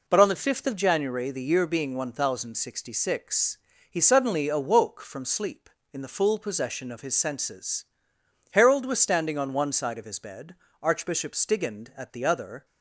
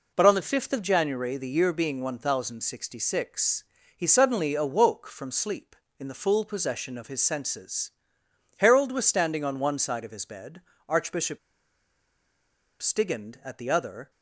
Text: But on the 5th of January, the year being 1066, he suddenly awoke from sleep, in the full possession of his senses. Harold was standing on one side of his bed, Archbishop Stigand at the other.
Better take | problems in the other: first | pauses between "Archbishop" and "Stigand"; strong; at 11.3 s; 1.4 s long

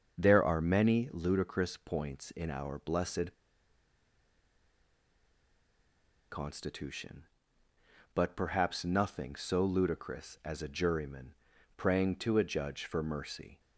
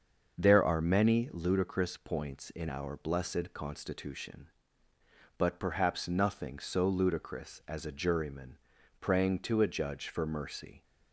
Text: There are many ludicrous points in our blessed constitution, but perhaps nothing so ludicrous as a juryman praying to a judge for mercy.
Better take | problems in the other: second | starts louder than the rest; until 1.2 s; 6.5 dB; also in the second // pauses between "blessed" and "constitution"; strong; at 3.3 s; 2.9 s long // pauses between "juryman" and "praying"; at 11.3 s; 0.42 s long; also in the second

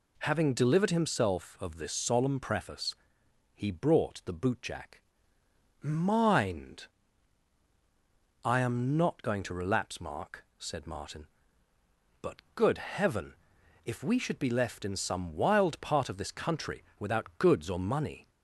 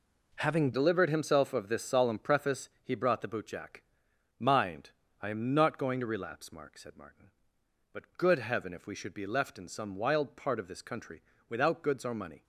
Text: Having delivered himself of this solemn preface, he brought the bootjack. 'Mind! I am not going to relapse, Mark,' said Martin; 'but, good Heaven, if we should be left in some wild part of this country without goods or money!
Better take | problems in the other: first | changes voice at "delivered"; from 0.7 s on; 11.7 s long // pauses between "country" and "without"; slight; at 11.2 s; 0.26 s long

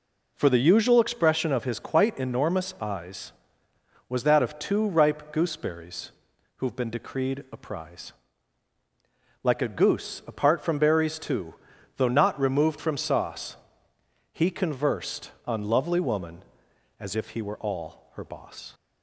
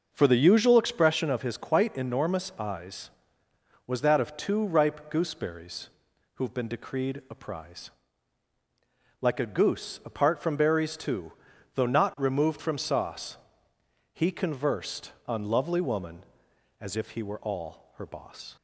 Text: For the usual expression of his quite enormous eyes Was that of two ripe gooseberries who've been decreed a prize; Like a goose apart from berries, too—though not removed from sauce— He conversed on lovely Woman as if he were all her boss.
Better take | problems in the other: first | starts louder than the rest; noticeable; until 1.3 s; 6 dB // pauses between "gooseberries" and "who've"; noticeable; at 5.8 s; 0.46 s long; noticeable in the first

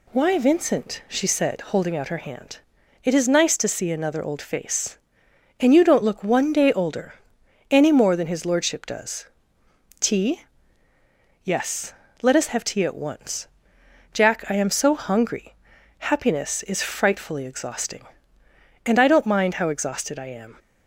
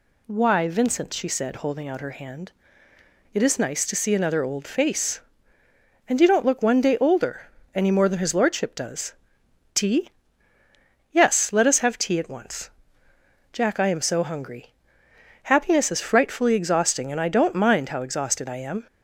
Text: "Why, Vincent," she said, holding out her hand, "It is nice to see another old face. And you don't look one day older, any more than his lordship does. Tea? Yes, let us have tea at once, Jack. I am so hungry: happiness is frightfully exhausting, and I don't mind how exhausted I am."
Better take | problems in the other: neither | none

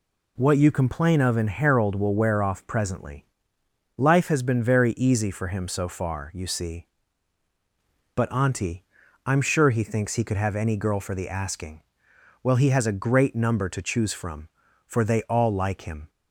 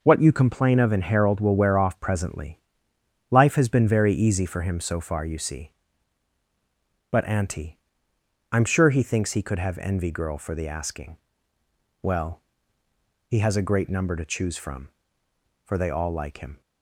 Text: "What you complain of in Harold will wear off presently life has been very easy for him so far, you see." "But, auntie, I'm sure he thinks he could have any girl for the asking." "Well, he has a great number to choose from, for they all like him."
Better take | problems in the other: first | pauses between "presently" and "life"; noticeable; at 2.5 s; 0.70 s long; noticeable in the first // says "envy" for "any"; at 9.7 s

